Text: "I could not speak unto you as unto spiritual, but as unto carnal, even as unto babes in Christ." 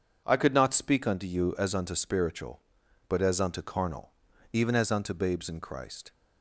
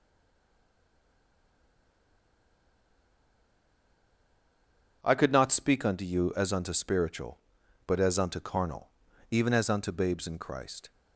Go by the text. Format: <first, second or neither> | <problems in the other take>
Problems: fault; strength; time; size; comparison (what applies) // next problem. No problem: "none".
first | stays silent before the first word; strong; until 5.0 s; 5.0 s long